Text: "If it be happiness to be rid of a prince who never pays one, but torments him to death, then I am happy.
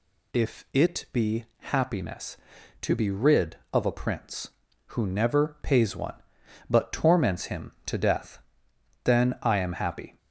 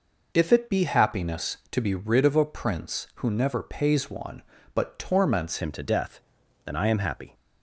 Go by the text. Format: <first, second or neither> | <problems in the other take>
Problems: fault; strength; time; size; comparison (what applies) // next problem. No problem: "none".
first | changes voice at "him"; from 5.6 s on; 1.7 s long